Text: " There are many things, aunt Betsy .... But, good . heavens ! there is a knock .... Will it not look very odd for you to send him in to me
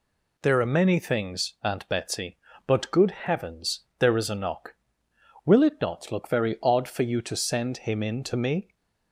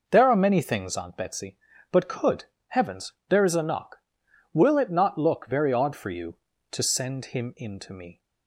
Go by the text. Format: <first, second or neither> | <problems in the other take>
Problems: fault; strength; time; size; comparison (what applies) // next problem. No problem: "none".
first | says "could" for "good"; at 2.0 s